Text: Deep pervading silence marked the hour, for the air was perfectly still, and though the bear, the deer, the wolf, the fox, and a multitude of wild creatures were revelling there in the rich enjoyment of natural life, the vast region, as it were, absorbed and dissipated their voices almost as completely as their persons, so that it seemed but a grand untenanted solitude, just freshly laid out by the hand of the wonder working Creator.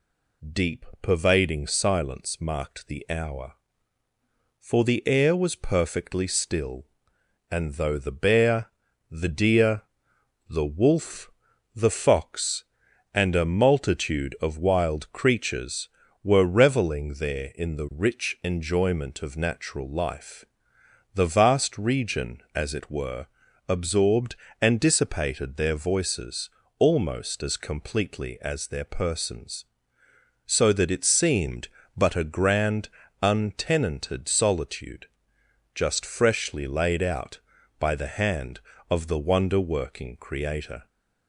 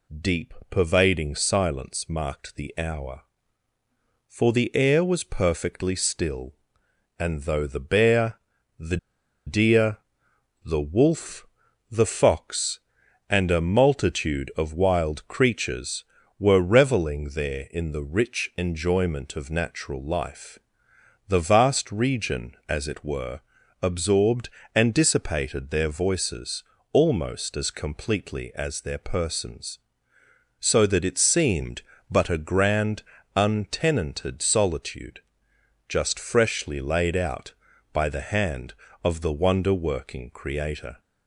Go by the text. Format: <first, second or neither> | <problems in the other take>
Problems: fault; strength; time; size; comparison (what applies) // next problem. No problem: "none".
first | pauses between "Deep" and "pervading"; slight; at 0.5 s; 0.16 s long; slight in the first // pauses between "the" and "deer"; noticeable; at 8.9 s; 0.49 s long // pauses between "voices" and "almost"; slight; at 26.6 s; 0.28 s long; slight in the first // pauses between "grand" and "untenanted"; slight; at 33.0 s; 0.34 s long; slight in the first